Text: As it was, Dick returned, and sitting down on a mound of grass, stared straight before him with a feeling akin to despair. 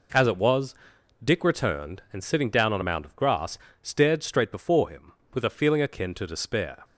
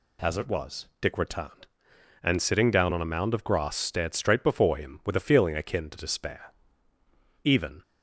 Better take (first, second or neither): first